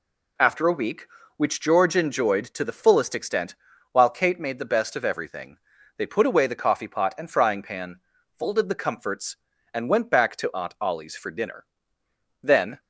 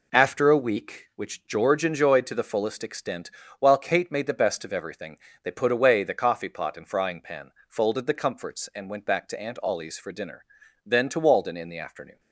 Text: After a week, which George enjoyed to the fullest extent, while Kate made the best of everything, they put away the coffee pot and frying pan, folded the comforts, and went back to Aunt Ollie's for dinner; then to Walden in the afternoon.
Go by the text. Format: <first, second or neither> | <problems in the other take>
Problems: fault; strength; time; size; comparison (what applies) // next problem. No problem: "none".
second | stops before "to Walden in the afternoon"; at 12.7 s